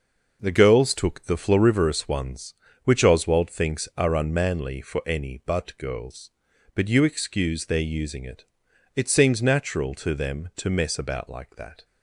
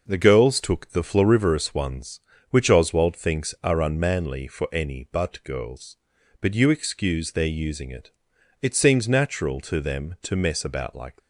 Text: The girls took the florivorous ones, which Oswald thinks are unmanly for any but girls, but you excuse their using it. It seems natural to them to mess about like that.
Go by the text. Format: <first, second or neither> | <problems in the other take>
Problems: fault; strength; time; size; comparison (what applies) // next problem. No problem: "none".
first | stops before "that"; at 11.1 s